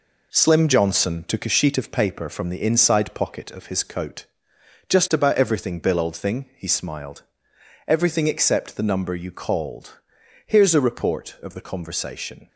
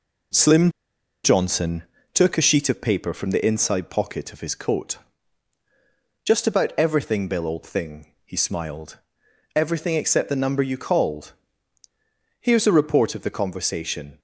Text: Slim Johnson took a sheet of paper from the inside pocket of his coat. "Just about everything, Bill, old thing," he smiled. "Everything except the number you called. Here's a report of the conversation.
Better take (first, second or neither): first